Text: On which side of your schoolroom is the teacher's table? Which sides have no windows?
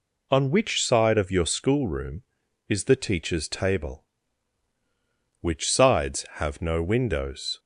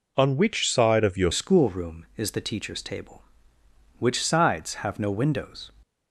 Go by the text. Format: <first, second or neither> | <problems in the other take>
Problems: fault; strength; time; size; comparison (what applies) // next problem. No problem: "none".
first | changes voice at "schoolroom"; from 1.3 s on; 4.4 s long